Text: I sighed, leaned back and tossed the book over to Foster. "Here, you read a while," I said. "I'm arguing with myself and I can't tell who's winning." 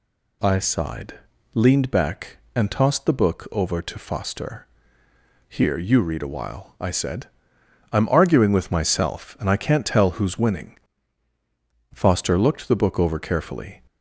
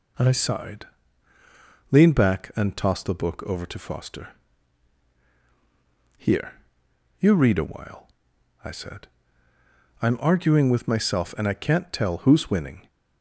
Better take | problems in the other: second | goes on to say "Foster looked the book over carefully"; strong; from 11.9 s on; 1.9 s long

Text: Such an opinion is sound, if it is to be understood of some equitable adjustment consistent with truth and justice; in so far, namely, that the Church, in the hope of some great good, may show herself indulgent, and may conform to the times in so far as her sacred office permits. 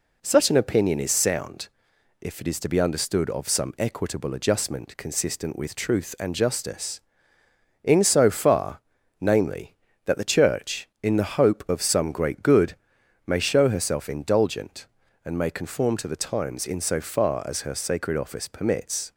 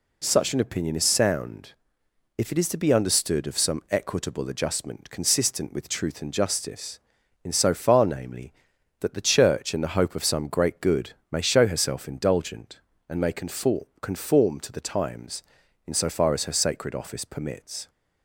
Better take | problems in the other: first | says "conform" twice; at 14.0 s

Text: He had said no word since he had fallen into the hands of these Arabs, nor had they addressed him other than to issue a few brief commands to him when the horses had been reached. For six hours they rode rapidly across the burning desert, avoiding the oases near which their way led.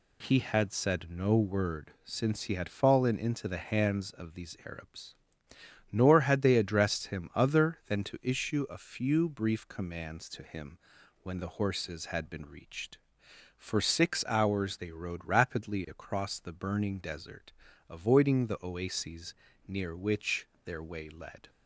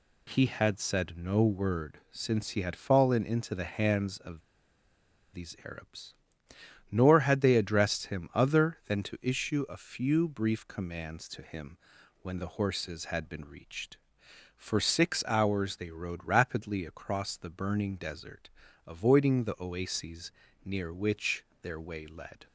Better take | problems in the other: first | pauses between "of" and "these"; noticeable; at 4.4 s; 0.93 s long // pauses between "him" and "when"; noticeable; at 11.7 s; 0.46 s long; noticeable in the first // pauses between "oases" and "near"; slight; at 20.3 s; 0.34 s long; slight in the first // pauses between "which" and "their"; slight; at 21.4 s; 0.16 s long; slight in the first

